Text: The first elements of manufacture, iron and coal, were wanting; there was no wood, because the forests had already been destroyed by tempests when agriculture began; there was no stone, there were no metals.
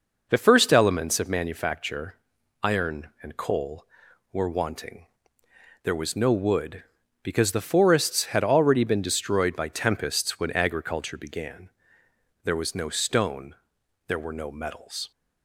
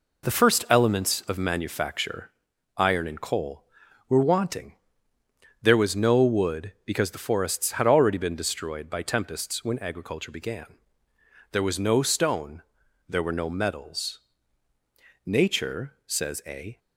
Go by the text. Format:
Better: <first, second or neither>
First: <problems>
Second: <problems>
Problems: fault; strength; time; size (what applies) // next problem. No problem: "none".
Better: first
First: none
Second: goes on to say "Nature says a"; from 15.2 s on; 1.5 s long